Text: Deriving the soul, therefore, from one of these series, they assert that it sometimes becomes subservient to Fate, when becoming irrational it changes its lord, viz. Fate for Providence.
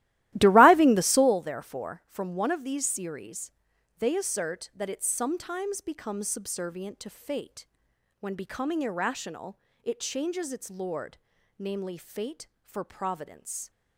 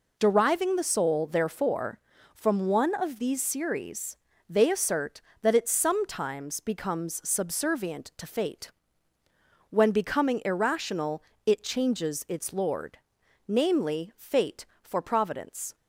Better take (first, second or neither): second